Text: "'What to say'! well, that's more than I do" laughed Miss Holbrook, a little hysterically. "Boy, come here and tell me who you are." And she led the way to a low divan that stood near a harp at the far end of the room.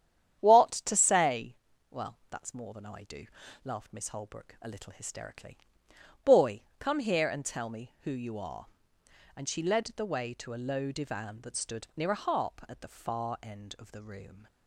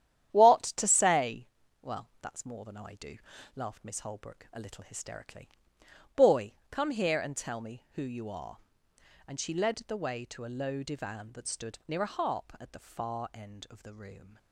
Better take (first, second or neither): first